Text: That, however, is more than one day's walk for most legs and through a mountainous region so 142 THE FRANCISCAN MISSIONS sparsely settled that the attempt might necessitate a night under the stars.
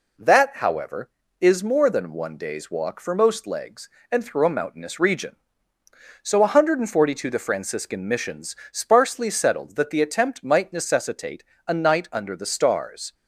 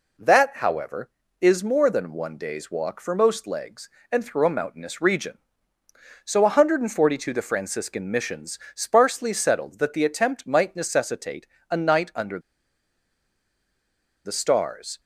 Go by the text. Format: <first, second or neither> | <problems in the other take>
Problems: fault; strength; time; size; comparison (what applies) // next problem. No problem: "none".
first | pauses between "MISSIONS" and "sparsely"; slight; at 8.5 s; 0.16 s long; slight in the first // pauses between "necessitate" and "a"; slight; at 11.4 s; 0.22 s long; slight in the first // pauses between "under" and "the"; strong; at 12.3 s; 1.8 s long